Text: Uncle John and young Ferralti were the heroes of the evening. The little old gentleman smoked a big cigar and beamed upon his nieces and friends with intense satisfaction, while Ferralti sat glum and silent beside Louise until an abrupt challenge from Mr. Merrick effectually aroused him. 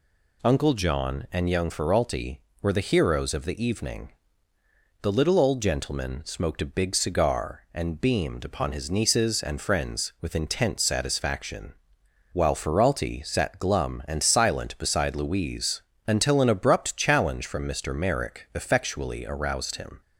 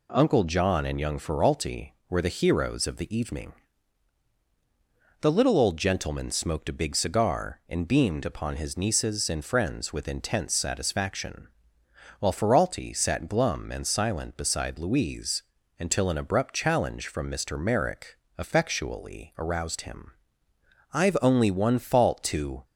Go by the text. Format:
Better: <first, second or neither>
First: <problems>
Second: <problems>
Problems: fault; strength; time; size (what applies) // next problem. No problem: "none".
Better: first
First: pauses between "Louise" and "until"; slight; at 15.8 s; 0.26 s long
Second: pauses between "Louise" and "until"; slight; at 15.4 s; 0.36 s long // pauses between "Merrick" and "effectually"; slight; at 18.1 s; 0.20 s long // goes on to say "I've only one fault to"; strong; from 20.9 s on; 1.7 s long